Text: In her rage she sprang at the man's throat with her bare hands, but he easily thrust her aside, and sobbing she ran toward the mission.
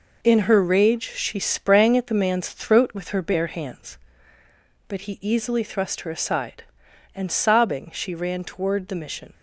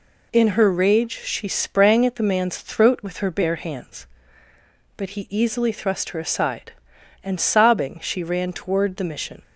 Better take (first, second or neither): second